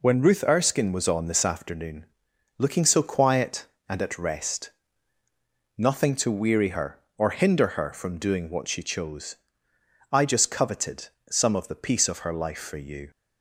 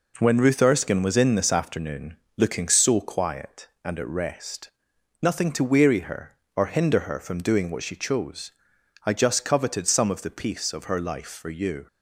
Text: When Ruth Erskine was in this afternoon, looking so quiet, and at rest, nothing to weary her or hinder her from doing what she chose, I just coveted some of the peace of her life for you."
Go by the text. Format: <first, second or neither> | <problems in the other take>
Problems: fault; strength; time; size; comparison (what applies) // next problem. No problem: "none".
second | says "on" for "in"; at 1.0 s // pauses between "coveted" and "some"; slight; at 11.0 s; 0.22 s long